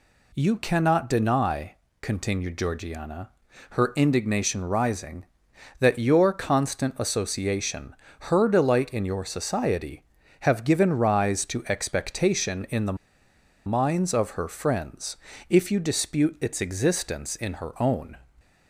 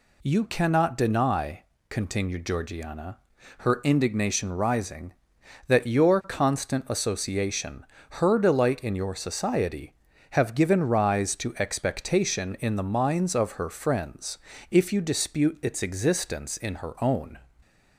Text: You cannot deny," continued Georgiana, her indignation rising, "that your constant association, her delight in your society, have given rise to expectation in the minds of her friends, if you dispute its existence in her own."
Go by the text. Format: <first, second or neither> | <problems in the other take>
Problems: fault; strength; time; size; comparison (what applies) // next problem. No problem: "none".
second | pauses between "the" and "minds"; noticeable; at 12.9 s; 0.71 s long